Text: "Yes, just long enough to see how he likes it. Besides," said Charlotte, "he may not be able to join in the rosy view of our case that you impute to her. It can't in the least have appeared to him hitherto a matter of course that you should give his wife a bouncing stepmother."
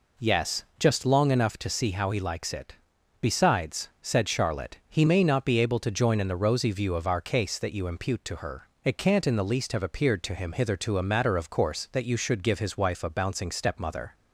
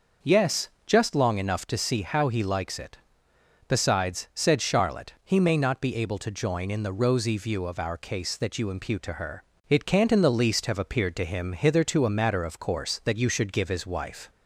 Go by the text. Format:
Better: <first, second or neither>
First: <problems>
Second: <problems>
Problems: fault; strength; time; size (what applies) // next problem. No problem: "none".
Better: first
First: none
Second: starts louder than the rest; noticeable; until 1.3 s; 6 dB // stops before "a bouncing stepmother"; at 14.2 s